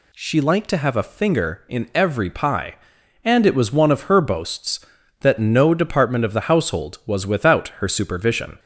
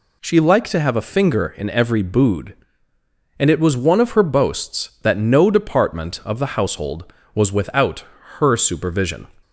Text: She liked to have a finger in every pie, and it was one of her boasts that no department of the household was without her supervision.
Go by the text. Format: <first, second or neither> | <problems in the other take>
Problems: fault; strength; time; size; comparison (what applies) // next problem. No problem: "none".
first | says "bood" for "pie"; at 2.0 s // pauses between "without" and "her"; slight; at 8.0 s; 0.34 s long